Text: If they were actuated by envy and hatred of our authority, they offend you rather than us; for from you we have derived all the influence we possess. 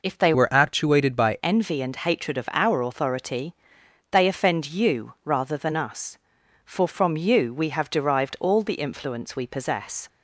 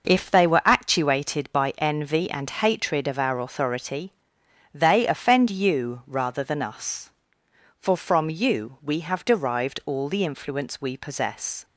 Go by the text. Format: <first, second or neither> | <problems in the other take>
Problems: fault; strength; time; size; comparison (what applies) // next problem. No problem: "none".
second | changes voice from "were" to "by"; from 0.3 to 1.3 s; 1.0 s long